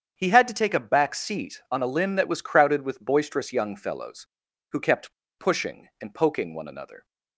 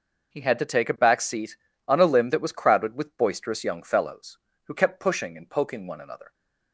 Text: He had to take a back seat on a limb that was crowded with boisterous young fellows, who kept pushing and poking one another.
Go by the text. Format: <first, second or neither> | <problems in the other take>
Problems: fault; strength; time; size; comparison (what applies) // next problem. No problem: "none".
second | starts louder than the rest; strong; until 1.1 s; 8 dB // pauses between "kept" and "pushing"; slight; at 5.1 s; 0.25 s long